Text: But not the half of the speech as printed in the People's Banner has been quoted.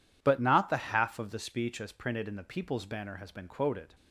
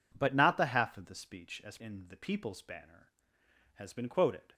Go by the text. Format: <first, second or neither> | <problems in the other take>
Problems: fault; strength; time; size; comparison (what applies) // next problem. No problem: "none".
first | skips "printed"; at 1.7 s